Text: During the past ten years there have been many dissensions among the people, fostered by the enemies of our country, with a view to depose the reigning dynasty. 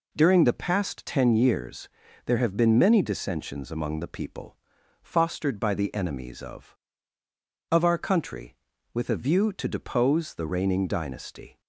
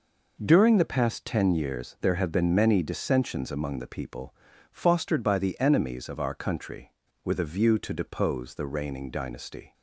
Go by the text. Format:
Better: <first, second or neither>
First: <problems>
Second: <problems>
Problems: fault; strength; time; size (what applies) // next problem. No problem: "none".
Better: second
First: pauses between "years" and "there"; at 1.8 s; 0.38 s long // says "of" twice; at 7.7 s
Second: none